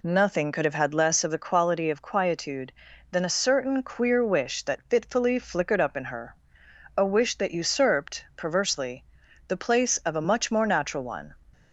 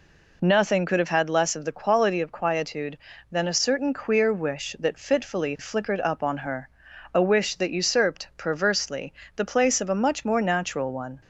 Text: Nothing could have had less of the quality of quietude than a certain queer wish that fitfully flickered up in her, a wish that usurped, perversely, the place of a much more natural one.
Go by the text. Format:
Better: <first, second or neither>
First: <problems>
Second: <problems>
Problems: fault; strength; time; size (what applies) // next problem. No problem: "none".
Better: first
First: none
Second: says "on" for "in"; at 6.2 s